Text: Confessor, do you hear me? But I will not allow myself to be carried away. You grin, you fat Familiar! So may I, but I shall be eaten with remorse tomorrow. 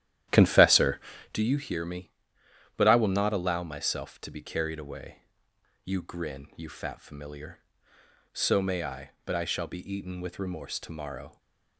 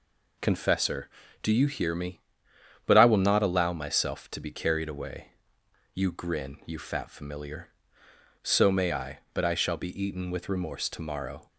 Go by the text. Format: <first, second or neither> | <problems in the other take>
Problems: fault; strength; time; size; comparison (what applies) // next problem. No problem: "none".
second | starts louder than the rest; strong; until 1.4 s; 11.5 dB // stays silent after the last word; slight; from 11.2 s on; 0.5 s long